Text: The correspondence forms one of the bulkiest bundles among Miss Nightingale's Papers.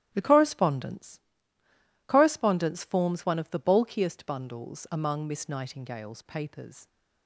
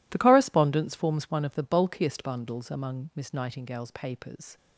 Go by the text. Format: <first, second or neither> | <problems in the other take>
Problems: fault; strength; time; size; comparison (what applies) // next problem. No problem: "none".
second | starts louder than the rest; strong; until 1.1 s; 12 dB // says "correspondence" twice; at 2.0 s